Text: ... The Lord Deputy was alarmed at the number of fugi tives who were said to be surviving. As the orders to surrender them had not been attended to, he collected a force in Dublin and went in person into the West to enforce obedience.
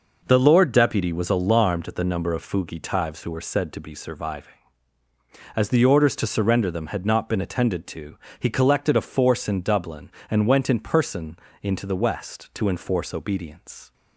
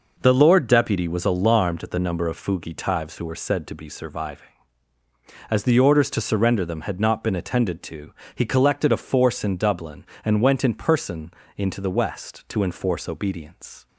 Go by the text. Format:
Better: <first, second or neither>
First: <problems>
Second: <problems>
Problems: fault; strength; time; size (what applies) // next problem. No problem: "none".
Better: neither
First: pauses between "person" and "into"; slight; at 11.3 s; 0.24 s long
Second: pauses between "person" and "into"; slight; at 11.3 s; 0.24 s long